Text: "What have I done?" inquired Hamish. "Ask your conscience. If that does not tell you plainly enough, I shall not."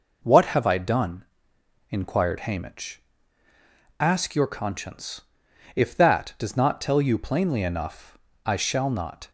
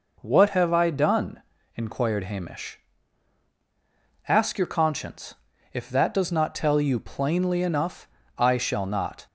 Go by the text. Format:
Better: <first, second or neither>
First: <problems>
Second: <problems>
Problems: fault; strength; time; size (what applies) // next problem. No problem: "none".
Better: neither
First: none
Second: none